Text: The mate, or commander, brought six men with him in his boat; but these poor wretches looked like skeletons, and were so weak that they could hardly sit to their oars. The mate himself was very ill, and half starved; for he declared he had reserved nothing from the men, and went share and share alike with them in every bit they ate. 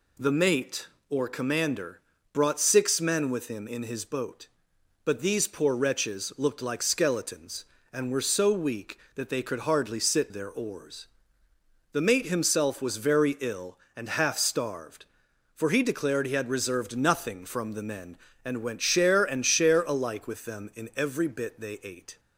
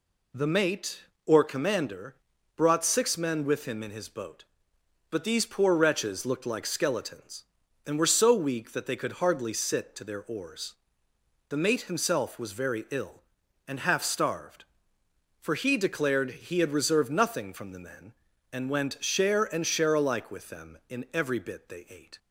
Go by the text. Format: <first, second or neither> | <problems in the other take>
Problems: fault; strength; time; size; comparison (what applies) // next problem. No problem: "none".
second | skips "to"; at 10.3 s